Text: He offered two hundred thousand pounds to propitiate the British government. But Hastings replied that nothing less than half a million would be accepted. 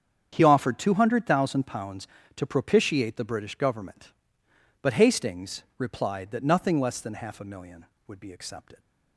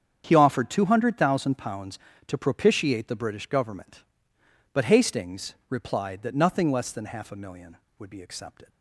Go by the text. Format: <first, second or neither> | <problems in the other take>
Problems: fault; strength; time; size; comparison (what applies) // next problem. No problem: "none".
neither | starts louder than the rest; strong; the same in both